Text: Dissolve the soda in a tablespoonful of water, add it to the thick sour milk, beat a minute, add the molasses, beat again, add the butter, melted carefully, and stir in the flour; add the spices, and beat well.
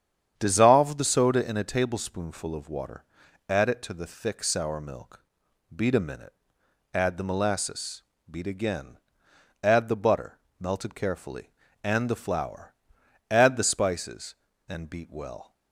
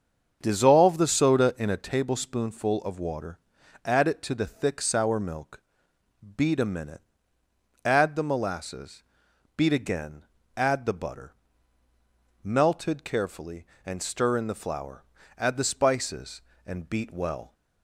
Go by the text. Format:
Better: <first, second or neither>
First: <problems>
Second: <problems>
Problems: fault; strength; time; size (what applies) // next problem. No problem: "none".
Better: second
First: starts louder than the rest; strong; until 1.3 s; 8.5 dB // skips "stir in"; at 12.0 s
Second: starts louder than the rest; until 1.4 s; 7 dB